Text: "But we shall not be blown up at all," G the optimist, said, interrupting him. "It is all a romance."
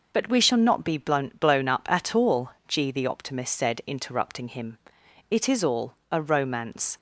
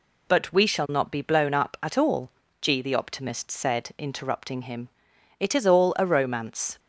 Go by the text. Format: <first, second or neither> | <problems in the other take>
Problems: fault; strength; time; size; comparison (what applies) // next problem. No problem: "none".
second | says "blown" twice; at 1.3 s // pauses between "all" and "a"; slight; at 5.9 s; 0.18 s long